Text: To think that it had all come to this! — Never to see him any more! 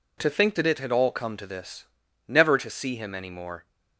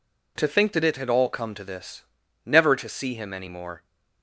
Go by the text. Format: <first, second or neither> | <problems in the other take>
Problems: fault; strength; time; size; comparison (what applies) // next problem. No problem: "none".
neither | none